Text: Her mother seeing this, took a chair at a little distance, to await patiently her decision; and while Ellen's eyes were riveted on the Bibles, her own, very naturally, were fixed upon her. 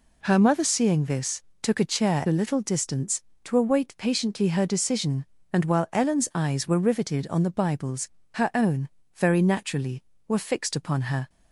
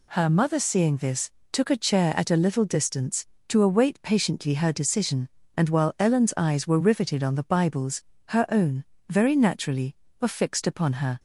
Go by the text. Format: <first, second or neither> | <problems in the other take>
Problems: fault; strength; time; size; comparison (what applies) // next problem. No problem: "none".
second | skips "at"; at 2.2 s